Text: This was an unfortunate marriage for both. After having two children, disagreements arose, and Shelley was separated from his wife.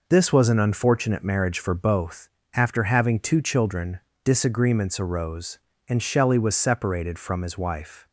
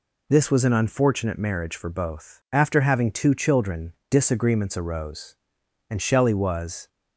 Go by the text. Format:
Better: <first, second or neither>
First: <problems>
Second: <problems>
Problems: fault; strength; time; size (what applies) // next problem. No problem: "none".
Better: first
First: none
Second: stops before "separated from his wife"; at 6.8 s